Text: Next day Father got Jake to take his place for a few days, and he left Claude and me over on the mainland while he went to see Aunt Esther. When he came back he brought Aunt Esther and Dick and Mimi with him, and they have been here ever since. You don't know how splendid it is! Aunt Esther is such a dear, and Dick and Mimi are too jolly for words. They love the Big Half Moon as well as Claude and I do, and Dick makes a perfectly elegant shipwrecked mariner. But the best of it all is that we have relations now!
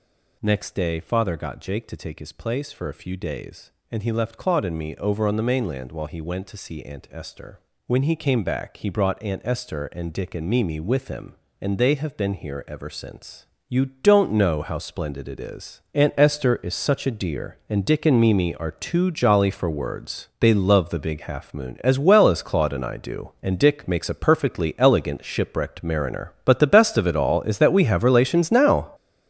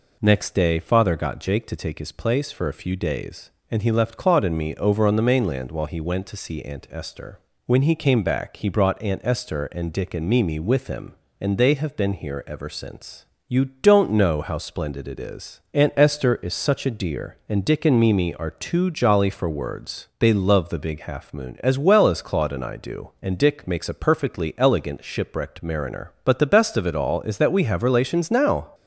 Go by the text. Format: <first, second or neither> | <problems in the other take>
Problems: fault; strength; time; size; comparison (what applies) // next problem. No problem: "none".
second | gets louder; strong; throughout; 9 dB